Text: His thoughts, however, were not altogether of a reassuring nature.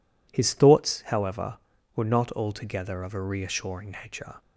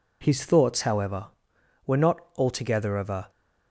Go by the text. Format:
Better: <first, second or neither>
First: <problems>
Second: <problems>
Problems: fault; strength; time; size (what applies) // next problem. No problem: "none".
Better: first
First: none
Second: pauses between "not" and "altogether"; slight; at 2.1 s; 0.16 s long // stops before "reassuring nature"; at 3.2 s